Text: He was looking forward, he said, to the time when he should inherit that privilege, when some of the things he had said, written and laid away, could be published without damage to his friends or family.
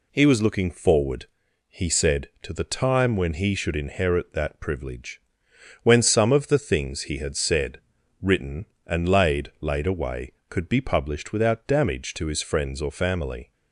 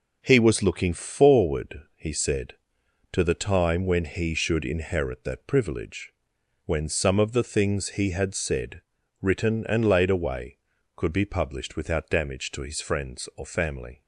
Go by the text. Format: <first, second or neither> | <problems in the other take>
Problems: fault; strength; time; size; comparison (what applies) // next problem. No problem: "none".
second | says "laid" twice; at 9.6 s